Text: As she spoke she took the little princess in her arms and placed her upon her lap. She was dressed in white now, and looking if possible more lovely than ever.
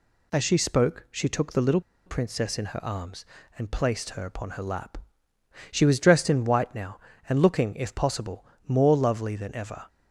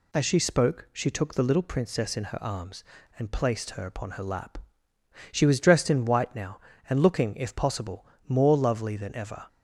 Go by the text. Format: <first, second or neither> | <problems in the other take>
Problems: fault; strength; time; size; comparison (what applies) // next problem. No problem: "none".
second | pauses between "little" and "princess"; slight; at 1.7 s; 0.26 s long // pauses between "possible" and "more"; slight; at 8.4 s; 0.22 s long; slight in the second